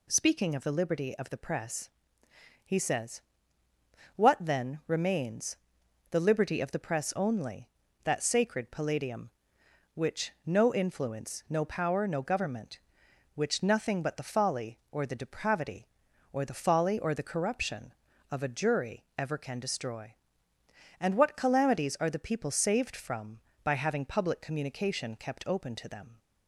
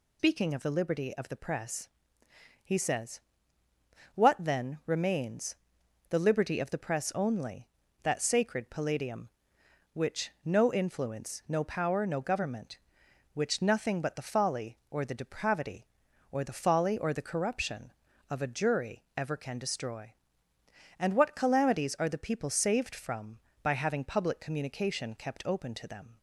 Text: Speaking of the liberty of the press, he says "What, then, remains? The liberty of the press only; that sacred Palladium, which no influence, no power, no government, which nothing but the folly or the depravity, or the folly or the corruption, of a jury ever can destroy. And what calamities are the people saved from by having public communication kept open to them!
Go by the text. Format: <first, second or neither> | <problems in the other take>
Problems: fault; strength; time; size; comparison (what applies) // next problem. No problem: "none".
first | loses the start of "Speaking"; at 0.1 s; 110 ms // pauses between "says" and "What"; noticeable; at 3.1 s; 0.94 s long; noticeable in the first // pauses between "which" and "no"; slight; at 10.2 s; 0.16 s long; slight in the first